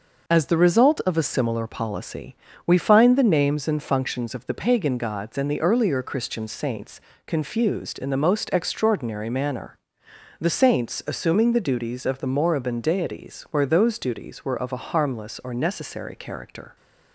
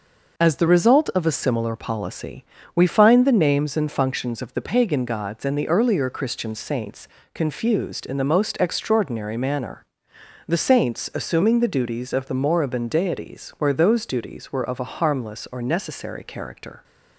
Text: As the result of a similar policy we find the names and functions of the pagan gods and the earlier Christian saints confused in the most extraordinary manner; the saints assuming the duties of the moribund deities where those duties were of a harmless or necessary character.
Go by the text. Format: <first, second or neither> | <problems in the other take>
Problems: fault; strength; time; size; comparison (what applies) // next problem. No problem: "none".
neither | pauses between "policy" and "we"; slight; the same in both // pauses between "saints" and "confused"; slight; the same in both